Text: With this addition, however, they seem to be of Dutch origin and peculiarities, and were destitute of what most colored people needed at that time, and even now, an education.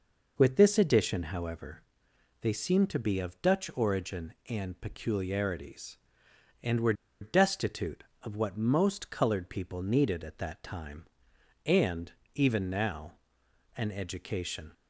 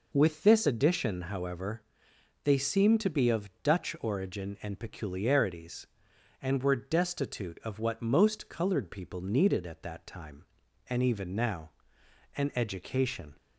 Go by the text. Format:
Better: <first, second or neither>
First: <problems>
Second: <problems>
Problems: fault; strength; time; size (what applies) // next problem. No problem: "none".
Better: second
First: pauses between "were" and "destitute"; slight; at 6.9 s; 0.27 s long // pauses between "and" and "even"; slight; at 12.1 s; 0.22 s long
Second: none